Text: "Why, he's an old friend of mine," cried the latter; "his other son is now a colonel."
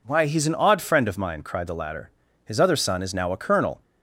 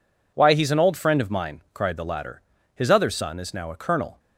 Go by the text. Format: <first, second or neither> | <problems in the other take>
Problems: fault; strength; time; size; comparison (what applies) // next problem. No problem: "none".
second | says "odd" for "old"; at 0.5 s